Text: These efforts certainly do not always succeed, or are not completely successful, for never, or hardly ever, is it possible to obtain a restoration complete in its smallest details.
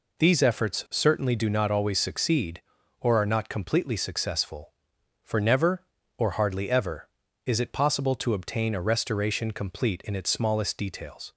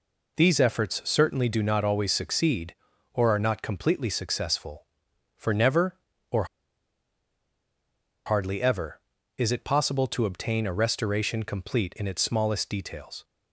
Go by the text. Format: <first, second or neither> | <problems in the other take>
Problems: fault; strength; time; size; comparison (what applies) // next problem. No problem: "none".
first | pauses between "or" and "hardly"; strong; at 6.4 s; 1.8 s long